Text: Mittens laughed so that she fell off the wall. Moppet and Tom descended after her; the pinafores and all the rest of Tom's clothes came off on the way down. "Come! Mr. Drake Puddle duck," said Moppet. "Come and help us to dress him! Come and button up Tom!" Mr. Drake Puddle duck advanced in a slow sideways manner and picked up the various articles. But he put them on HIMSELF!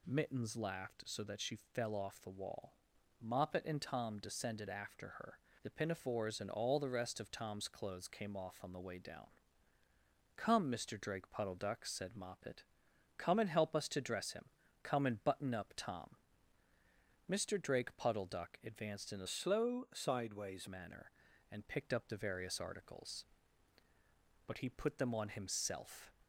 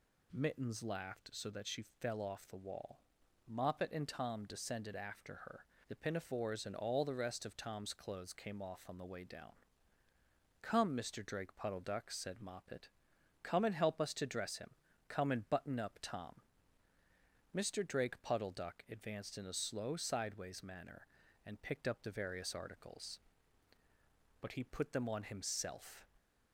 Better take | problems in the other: second | changes voice from "slow" to "sideways"; from 19.2 to 20.6 s; 1.4 s long

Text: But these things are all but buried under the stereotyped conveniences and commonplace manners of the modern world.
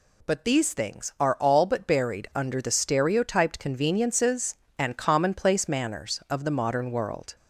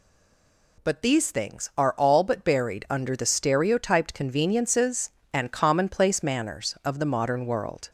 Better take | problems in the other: first | stays silent before the first word; slight; until 0.7 s; 0.7 s long

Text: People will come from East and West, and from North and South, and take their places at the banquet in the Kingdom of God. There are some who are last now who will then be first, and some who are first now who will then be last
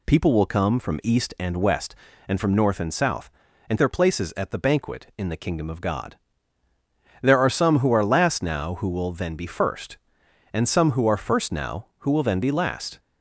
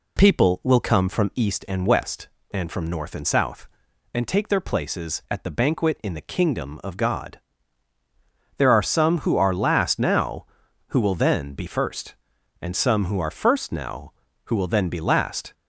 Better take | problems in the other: second | skips "take"; at 3.7 s

